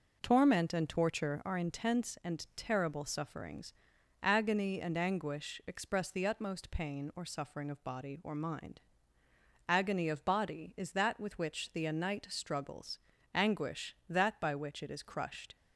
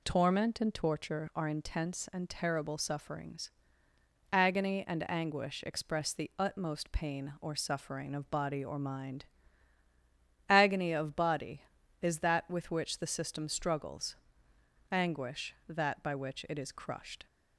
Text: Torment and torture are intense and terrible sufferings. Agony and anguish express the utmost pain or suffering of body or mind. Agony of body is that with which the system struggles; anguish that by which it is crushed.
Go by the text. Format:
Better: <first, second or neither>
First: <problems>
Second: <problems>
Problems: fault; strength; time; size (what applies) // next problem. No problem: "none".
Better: second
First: says "anite" for "system"; at 11.8 s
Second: none